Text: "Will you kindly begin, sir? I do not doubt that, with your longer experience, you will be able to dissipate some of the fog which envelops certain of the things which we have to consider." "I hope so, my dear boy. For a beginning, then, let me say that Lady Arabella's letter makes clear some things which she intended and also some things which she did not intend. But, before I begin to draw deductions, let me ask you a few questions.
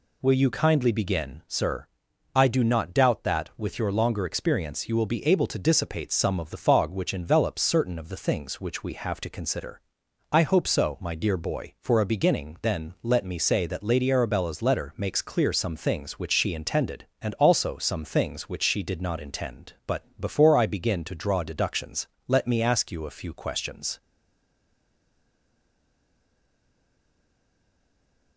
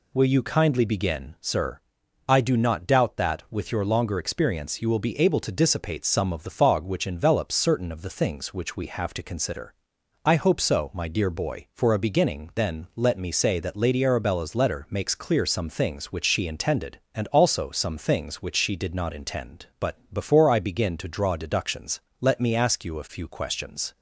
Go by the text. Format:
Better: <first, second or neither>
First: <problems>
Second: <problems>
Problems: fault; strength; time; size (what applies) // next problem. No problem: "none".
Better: second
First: stays silent after the last word; strong; from 24.0 s on; 4.3 s long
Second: none